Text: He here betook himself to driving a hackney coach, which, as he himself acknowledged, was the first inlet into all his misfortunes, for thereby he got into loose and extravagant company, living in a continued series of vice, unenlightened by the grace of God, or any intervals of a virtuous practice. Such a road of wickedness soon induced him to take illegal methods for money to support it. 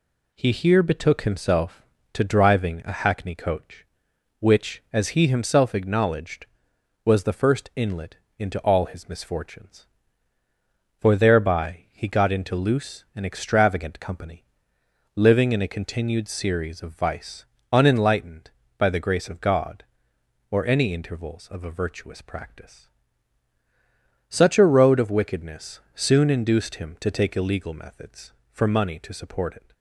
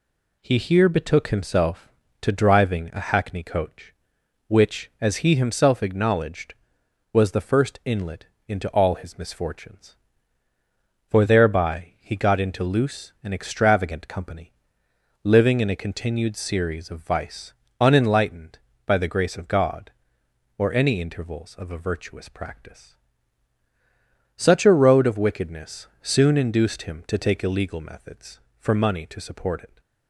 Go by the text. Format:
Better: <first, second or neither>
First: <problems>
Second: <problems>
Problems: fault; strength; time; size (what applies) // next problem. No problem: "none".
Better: neither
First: pauses between "inlet" and "into"; slight; at 8.1 s; 0.20 s long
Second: pauses between "inlet" and "into"; slight; at 8.2 s; 0.20 s long